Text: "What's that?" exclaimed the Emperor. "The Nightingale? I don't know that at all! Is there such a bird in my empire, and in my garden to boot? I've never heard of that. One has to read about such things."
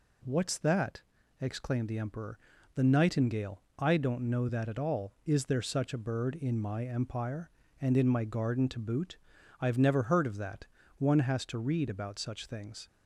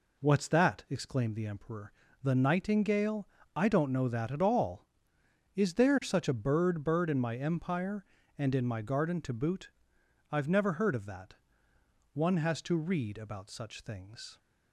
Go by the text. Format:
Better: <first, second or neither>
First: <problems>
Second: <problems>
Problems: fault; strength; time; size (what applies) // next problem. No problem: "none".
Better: first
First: none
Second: says "bird" twice; at 6.8 s